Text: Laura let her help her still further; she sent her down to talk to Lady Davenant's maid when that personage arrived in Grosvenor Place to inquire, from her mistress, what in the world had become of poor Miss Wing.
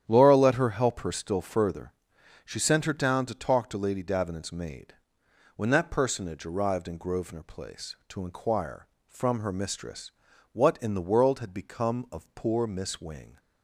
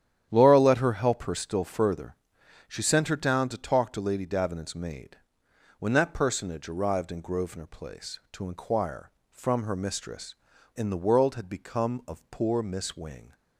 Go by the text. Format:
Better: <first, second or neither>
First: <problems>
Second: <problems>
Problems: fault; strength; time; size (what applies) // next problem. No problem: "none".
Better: first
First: starts louder than the rest; strong; until 1.0 s; 10 dB // pauses between "maid" and "when"; noticeable; at 4.9 s; 0.62 s long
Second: starts louder than the rest; strong; until 1.3 s; 10 dB // pauses between "maid" and "when"; noticeable; at 5.1 s; 0.62 s long // skips "what"; at 10.5 s